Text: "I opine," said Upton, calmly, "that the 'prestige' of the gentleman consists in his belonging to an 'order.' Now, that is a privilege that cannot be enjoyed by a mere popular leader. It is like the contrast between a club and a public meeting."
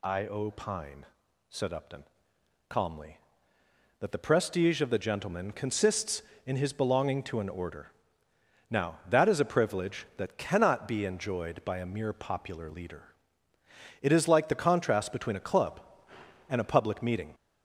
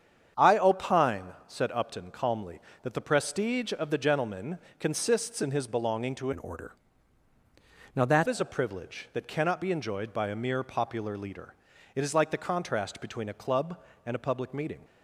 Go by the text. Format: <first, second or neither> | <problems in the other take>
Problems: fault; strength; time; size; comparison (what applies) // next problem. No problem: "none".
first | starts louder than the rest; strong; until 1.5 s; 8 dB // pauses between "gentleman" and "consists"; slight; at 4.5 s; 0.22 s long // changes voice from "an" to "that"; from 6.3 to 8.2 s; 1.9 s long